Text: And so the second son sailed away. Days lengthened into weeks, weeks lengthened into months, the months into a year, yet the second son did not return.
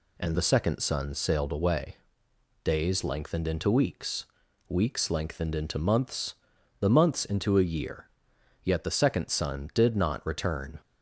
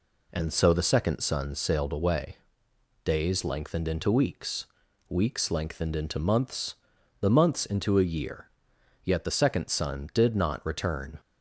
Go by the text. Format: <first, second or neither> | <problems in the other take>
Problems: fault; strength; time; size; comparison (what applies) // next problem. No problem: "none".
second | skips "so"; at 0.3 s